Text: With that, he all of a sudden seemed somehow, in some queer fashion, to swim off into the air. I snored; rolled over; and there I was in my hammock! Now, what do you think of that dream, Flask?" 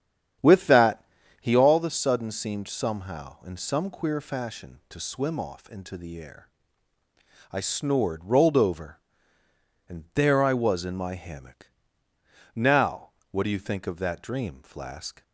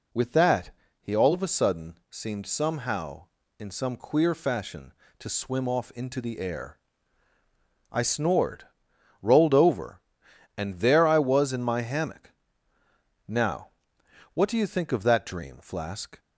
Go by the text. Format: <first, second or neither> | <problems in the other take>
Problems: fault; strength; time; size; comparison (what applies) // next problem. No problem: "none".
second | starts louder than the rest; strong; until 1.7 s; 9 dB